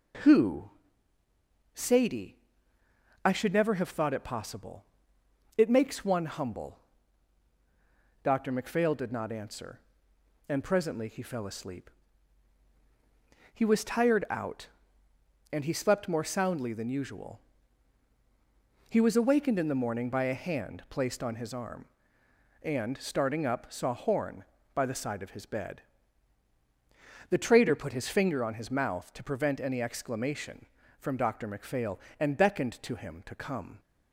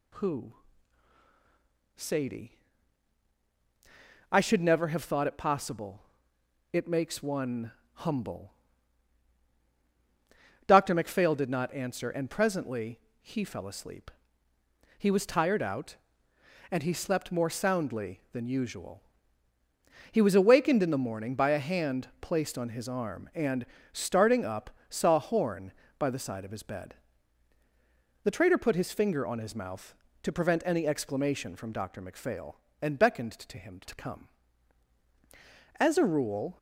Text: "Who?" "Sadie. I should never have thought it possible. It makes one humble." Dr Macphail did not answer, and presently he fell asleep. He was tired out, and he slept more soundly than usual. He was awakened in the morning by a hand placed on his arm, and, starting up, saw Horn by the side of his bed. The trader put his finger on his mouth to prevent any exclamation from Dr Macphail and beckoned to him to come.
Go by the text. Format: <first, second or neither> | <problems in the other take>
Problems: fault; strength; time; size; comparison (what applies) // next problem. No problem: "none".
first | pauses between "one" and "humble"; slight; at 7.7 s; 0.22 s long // pauses between "presently" and "he"; slight; at 12.9 s; 0.22 s long // goes on to say "As a rule"; noticeable; from 35.7 s on; 0.82 s long